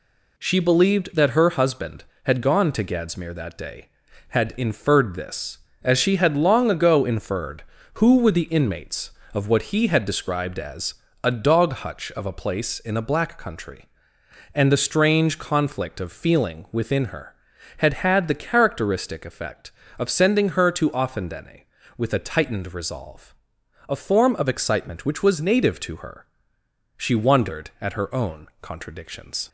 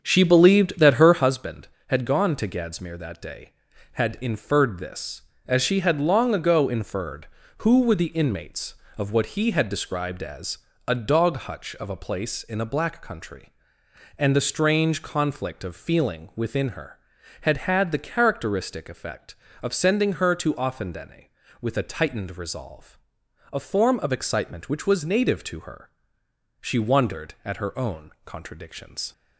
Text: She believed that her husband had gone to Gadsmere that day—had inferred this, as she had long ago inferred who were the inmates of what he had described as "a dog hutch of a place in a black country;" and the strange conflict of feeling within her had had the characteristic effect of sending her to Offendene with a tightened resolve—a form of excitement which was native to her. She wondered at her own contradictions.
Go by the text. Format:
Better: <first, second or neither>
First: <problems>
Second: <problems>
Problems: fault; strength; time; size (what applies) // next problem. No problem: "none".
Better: first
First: pauses between "as" and "a"; slight; at 10.9 s; 0.30 s long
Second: starts louder than the rest; until 1.4 s; 7 dB // pauses between "as" and "a"; slight; at 10.5 s; 0.30 s long